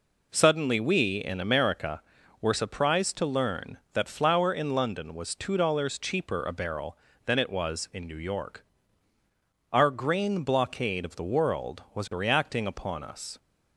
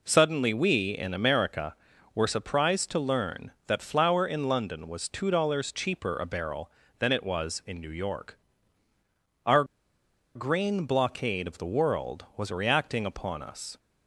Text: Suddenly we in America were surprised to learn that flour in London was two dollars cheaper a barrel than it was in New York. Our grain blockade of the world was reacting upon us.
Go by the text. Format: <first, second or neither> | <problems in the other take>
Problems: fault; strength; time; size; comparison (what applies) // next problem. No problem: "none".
first | pauses between "Our" and "grain"; noticeable; at 9.6 s; 0.71 s long